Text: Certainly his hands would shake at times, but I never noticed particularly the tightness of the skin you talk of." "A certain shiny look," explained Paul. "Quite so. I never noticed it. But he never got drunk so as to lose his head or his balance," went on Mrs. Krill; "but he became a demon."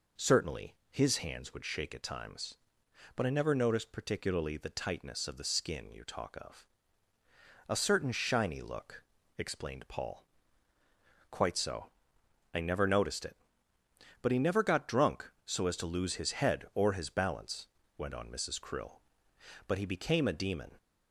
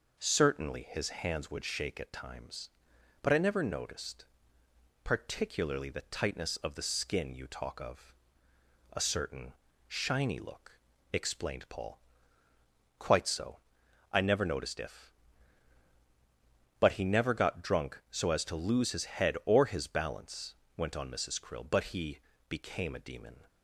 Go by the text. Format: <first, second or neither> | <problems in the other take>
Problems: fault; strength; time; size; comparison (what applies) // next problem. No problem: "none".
first | pauses between "noticed" and "particularly"; noticeable; at 4.2 s; 0.78 s long // pauses between "certain" and "shiny"; slight; at 9.5 s; 0.34 s long // says "if" for "it"; at 14.8 s // pauses between "he" and "became"; slight; at 22.1 s; 0.30 s long